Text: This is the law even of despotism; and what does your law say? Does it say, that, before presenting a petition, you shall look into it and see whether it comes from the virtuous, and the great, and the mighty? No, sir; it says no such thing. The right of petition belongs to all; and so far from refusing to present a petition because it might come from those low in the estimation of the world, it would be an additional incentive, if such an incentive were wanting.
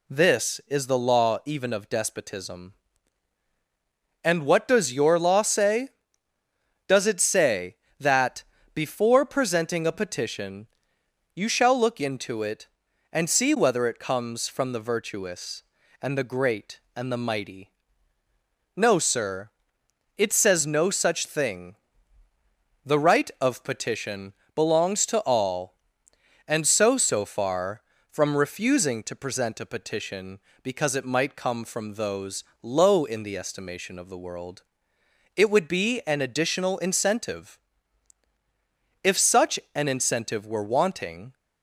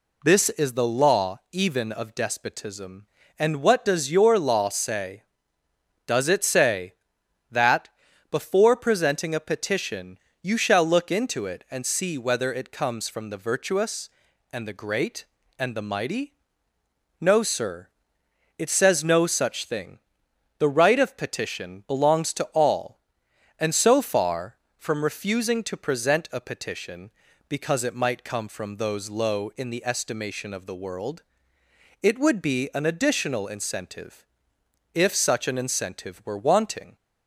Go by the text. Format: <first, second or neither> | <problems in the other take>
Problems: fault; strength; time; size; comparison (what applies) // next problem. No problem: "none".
second | pauses between "petition" and "belongs"; slight; at 24.3 s; 0.24 s long // says "so" twice; at 26.9 s // pauses between "those" and "low"; slight; at 32.4 s; 0.20 s long // pauses between "such" and "an"; slight; at 39.5 s; 0.16 s long